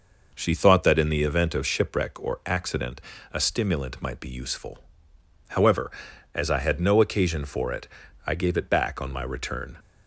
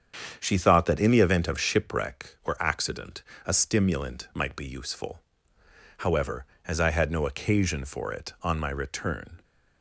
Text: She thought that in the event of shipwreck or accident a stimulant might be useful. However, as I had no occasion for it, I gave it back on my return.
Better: first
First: pauses between "accident" and "a"; slight; at 3.0 s; 0.32 s long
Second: starts louder than the rest; strong; until 1.3 s; 8 dB // pauses between "accident" and "a"; slight; at 3.2 s; 0.22 s long // skips "I gave it back"; at 8.3 s

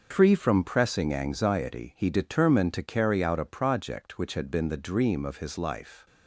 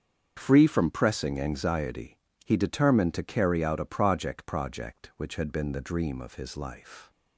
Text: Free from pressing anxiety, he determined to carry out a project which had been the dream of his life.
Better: first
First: starts louder than the rest; until 1.1 s; 6 dB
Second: starts louder than the rest; strong; until 1.3 s; 7 dB // says "project" twice; at 4.4 s

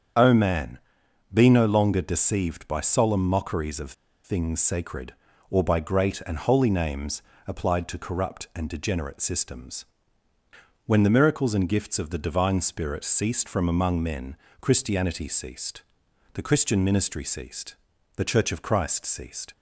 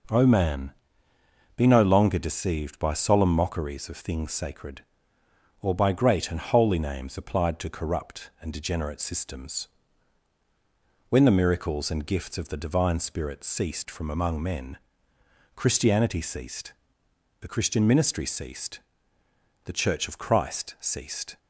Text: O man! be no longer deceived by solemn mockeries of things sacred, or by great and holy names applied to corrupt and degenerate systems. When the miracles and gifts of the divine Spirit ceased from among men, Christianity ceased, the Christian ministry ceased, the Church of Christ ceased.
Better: second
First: starts louder than the rest; strong; until 1.6 s; 7.5 dB // pauses between "of" and "things"; slight; at 3.9 s; 0.32 s long // pauses between "names" and "applied"; slight; at 7.2 s; 0.26 s long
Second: none

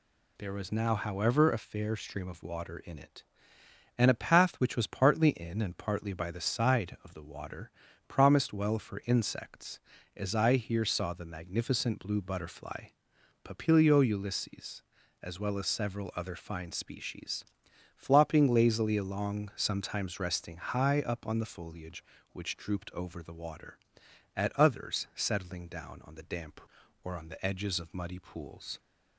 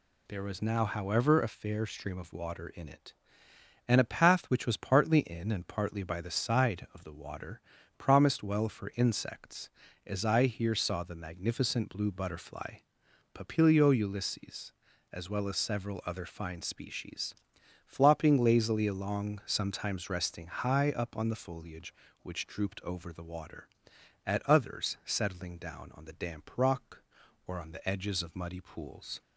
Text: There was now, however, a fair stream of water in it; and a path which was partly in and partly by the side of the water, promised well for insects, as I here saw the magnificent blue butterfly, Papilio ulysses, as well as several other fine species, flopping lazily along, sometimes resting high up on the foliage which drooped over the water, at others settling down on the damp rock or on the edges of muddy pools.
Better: second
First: skips "rock"; at 26.8 s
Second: none

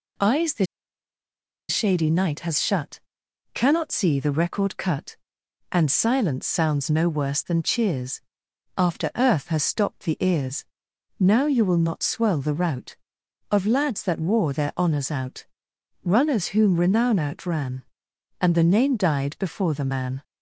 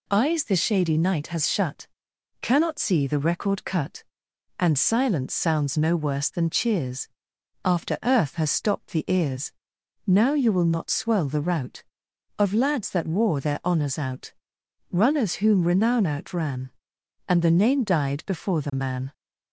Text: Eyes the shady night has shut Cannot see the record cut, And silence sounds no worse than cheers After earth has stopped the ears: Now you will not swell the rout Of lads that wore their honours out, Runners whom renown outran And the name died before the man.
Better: second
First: pauses between "the" and "shady"; at 0.6 s; 1.0 s long // pauses between "shut" and "Cannot"; noticeable; at 3.0 s; 0.52 s long // pauses between "cheers" and "After"; noticeable; at 8.2 s; 0.56 s long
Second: pauses between "shut" and "Cannot"; noticeable; at 1.8 s; 0.52 s long // pauses between "cheers" and "After"; noticeable; at 7.0 s; 0.56 s long

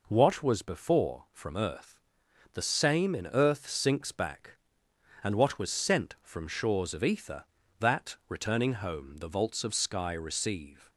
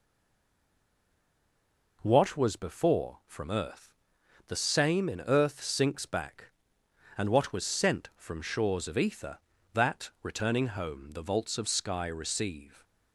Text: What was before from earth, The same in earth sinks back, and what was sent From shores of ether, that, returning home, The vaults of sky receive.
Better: first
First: none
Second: stays silent before the first word; noticeable; until 2.0 s; 2.0 s long

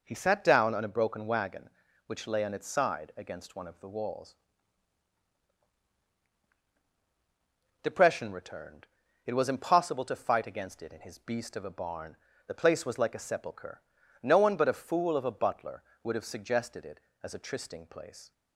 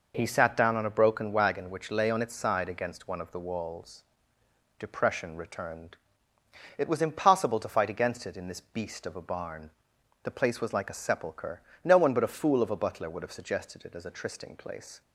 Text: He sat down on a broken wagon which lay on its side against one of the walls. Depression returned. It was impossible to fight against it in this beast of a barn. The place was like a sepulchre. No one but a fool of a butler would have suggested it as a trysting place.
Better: second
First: says "his" for "this"; at 11.0 s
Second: none

